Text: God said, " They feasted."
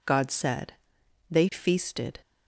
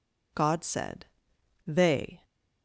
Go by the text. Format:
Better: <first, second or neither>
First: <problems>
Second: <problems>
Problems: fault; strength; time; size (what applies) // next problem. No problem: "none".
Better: first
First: none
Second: stops before "feasted"; at 2.2 s